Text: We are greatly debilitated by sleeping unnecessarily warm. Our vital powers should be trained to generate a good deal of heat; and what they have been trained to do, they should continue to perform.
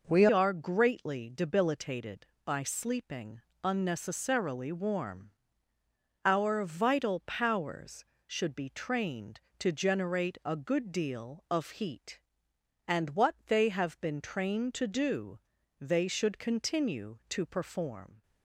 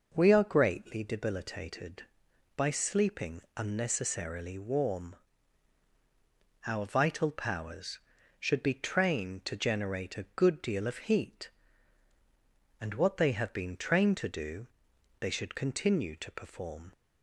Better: second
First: changes voice at "are"; from 0.3 s on; 17.9 s long // pauses between "sleeping" and "unnecessarily"; slight; at 3.4 s; 0.24 s long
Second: pauses between "sleeping" and "unnecessarily"; slight; at 3.3 s; 0.16 s long

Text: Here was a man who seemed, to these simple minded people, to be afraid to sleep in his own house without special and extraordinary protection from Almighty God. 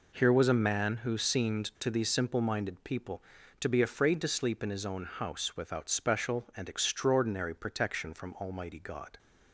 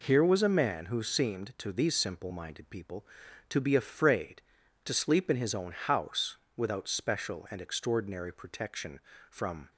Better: first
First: none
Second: pauses between "house" and "without"; slight; at 6.3 s; 0.18 s long // stops before "Almighty God"; at 9.7 s

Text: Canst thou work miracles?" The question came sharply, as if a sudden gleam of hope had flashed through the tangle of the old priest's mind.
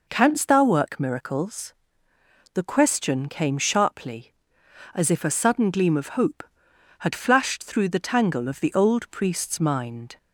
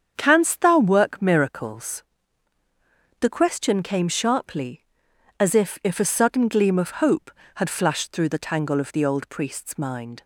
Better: first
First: none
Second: starts louder than the rest; strong; until 1.1 s; 8 dB // says "if" twice; at 5.8 s

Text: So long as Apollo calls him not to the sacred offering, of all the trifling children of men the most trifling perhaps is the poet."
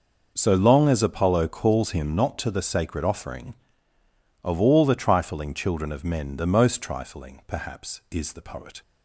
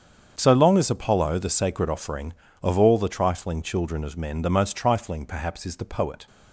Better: first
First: none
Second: starts louder than the rest; strong; until 1.3 s; 7.5 dB // skips "calls him not to"; at 1.3 s

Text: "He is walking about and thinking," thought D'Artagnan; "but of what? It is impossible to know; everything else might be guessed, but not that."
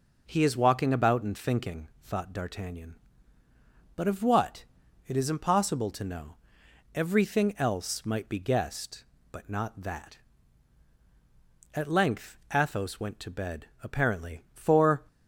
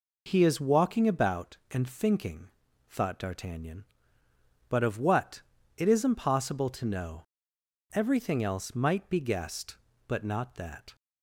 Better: second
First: goes on to say "At length Athos went to bed apparently for"; strong; from 11.7 s on; 3.3 s long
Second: none

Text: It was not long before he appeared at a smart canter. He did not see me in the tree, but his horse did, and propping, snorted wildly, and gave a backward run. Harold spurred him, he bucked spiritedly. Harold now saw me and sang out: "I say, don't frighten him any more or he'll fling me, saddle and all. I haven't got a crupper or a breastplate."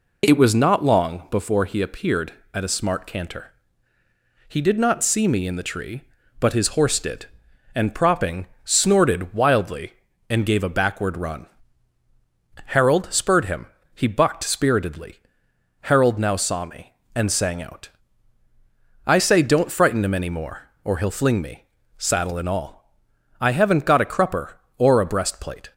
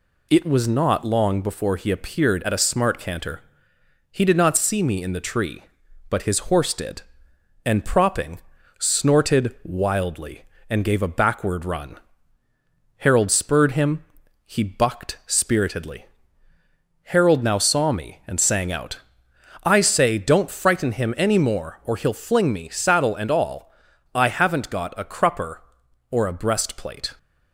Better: neither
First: none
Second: none

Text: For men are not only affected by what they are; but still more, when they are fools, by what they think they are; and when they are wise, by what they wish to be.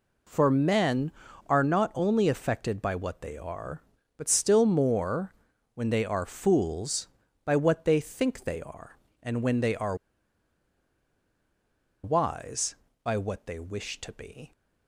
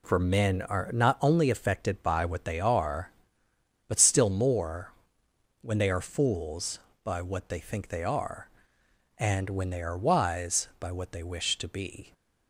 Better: second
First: pauses between "are" and "wise"; strong; at 9.9 s; 2.0 s long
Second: none

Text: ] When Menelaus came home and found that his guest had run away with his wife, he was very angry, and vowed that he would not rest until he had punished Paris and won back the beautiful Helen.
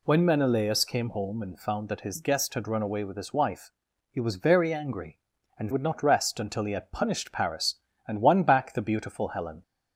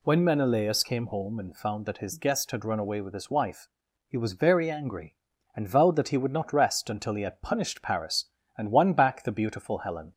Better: second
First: skips "vowed that he"; at 5.7 s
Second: none

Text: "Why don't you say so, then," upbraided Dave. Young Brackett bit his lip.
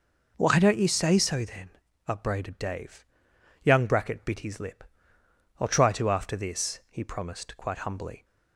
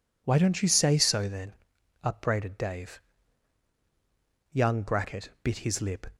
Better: second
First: goes on to say "I'll try to after this he promised quite humbly"; strong; from 5.5 s on; 2.6 s long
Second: none

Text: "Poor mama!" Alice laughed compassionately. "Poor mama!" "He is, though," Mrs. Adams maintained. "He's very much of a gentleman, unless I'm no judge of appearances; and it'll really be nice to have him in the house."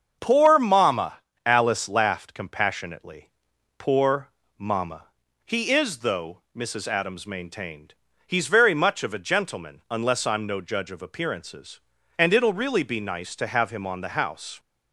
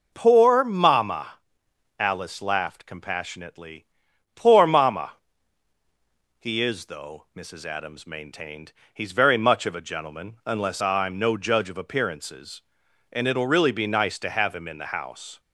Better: second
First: starts louder than the rest; until 1.2 s; 7 dB // pauses between "Poor" and "mama"; slight; at 4.3 s; 0.26 s long // says "on" for "in"; at 13.8 s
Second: none

